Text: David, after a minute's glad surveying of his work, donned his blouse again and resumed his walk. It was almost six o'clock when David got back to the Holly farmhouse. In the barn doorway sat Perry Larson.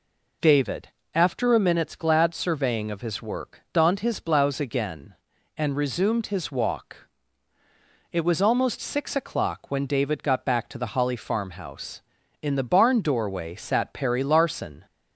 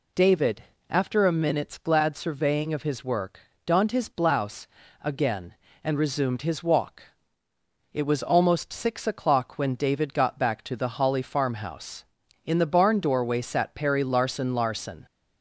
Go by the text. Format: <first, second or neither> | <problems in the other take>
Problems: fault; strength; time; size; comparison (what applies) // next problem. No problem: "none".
first | pauses between "blouse" and "again"; at 4.6 s; 0.38 s long // says "Larson" twice; at 14.5 s